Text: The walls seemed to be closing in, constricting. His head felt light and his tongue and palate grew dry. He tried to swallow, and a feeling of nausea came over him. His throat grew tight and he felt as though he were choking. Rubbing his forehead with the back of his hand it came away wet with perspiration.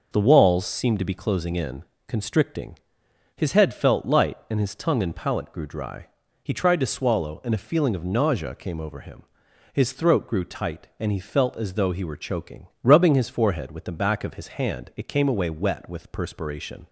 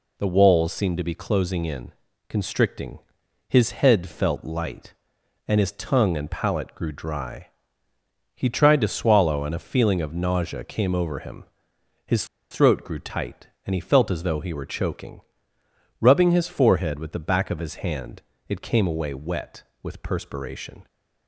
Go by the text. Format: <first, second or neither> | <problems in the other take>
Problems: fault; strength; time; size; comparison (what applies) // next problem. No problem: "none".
first | pauses between "His" and "throat"; slight; at 12.2 s; 0.26 s long // pauses between "hand" and "it"; slight; at 18.2 s; 0.26 s long